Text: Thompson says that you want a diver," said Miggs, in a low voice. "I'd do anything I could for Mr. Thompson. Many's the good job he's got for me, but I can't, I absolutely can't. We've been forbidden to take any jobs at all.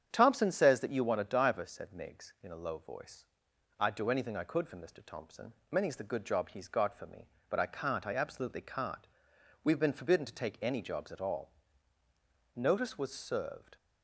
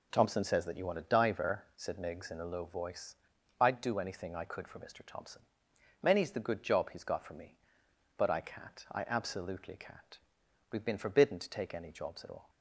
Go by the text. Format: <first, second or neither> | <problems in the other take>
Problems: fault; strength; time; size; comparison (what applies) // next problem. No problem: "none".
second | starts louder than the rest; strong; until 1.1 s; 8.5 dB // goes on to say "Notice was served"; noticeable; from 12.5 s on; 1.2 s long